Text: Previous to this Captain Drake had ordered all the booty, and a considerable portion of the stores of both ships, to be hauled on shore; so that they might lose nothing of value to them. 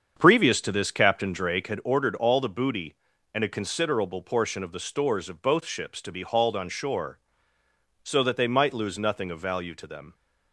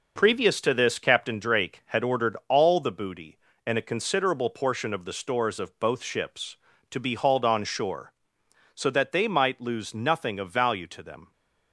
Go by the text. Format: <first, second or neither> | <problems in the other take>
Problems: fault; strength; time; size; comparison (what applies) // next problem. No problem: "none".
second | starts louder than the rest; strong; until 1.7 s; 7.5 dB